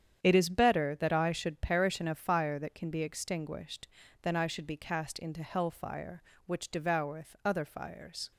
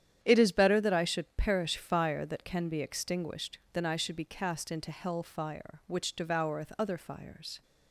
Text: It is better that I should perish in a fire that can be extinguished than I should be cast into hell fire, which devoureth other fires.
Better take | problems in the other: first | starts louder than the rest; strong; until 1.2 s; 10 dB; strong in the first // skips "in a"; at 1.7 s

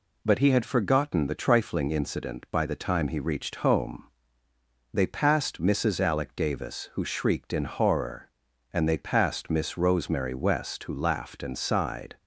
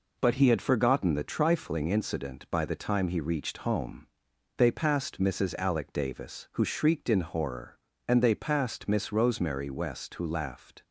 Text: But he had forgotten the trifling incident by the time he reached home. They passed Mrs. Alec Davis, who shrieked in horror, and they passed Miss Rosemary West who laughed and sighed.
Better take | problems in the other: first | stops before "and sighed"; at 10.8 s

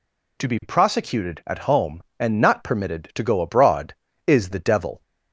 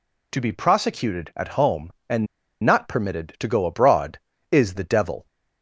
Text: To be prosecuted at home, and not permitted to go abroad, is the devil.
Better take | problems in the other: first | pauses between "and" and "not"; at 2.2 s; 0.37 s long

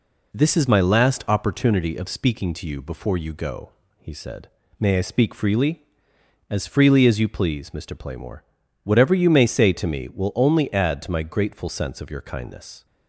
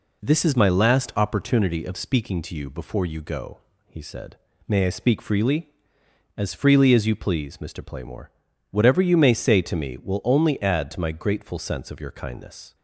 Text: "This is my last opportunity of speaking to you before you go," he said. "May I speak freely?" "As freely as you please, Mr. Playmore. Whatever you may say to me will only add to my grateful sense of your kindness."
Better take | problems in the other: neither | none

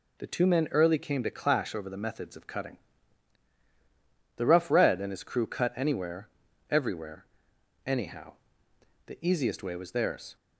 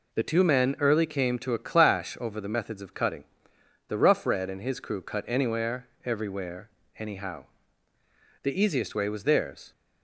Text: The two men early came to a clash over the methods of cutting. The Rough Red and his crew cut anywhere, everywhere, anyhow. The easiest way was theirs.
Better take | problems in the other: second | skips "a"; at 1.2 s

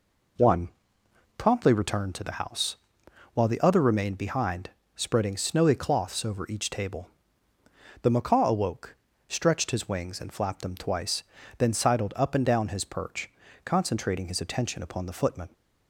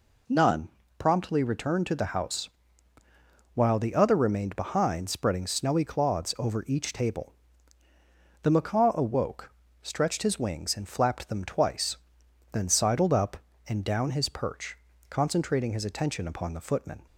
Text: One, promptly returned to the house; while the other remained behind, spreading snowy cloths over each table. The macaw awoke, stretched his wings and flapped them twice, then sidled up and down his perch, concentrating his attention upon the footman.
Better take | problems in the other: first | says "None" for "One"; at 0.2 s

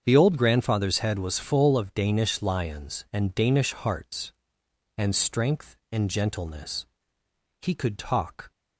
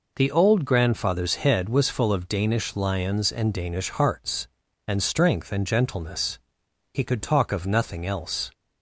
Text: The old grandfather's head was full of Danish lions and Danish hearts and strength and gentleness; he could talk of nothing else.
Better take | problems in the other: second | starts louder than the rest; strong; until 1.0 s; 7.5 dB // stops before "of nothing else"; at 8.5 s

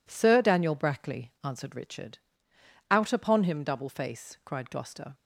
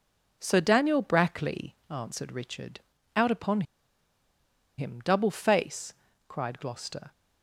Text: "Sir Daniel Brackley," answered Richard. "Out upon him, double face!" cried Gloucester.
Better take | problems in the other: first | pauses between "upon" and "him"; at 3.6 s; 1.1 s long

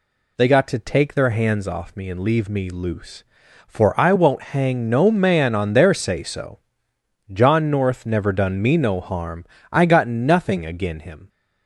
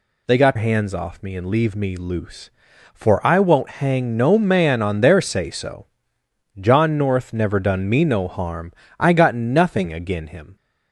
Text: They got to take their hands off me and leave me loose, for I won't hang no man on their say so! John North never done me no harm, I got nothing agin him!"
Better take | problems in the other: first | skips "to take their"; at 0.5 s

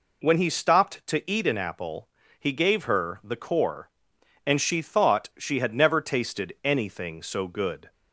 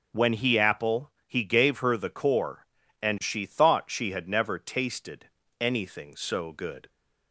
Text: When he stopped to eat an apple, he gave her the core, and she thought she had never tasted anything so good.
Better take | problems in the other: first | skips "stopped to eat an"; at 0.5 s // pauses between "tasted" and "anything"; slight; at 5.2 s; 0.32 s long

